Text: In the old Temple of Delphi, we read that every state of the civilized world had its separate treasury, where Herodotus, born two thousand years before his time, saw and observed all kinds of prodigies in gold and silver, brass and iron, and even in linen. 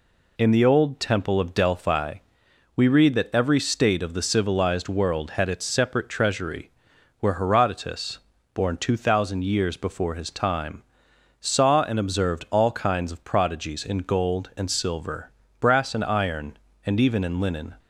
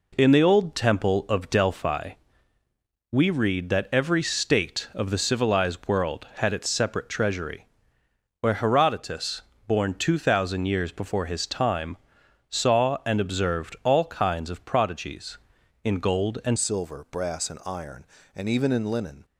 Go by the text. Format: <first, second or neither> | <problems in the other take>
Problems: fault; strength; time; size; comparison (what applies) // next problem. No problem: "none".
first | changes voice at "silver"; from 16.5 s on; 2.7 s long